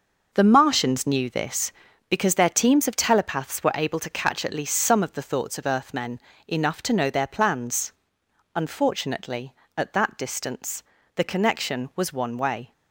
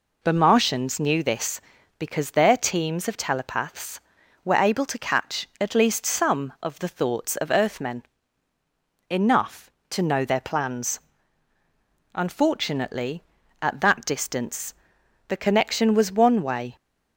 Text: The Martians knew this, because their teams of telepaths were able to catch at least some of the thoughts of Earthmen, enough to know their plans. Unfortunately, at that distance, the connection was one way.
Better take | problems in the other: second | gets quieter; strong; throughout; 8 dB

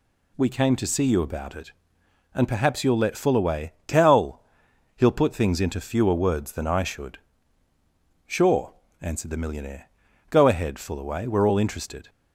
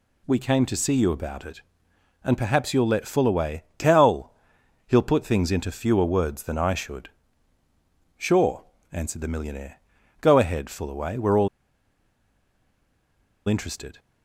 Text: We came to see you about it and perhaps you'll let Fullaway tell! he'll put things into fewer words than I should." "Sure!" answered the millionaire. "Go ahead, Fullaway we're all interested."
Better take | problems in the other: first | pauses between "all" and "interested"; strong; at 11.4 s; 2.0 s long

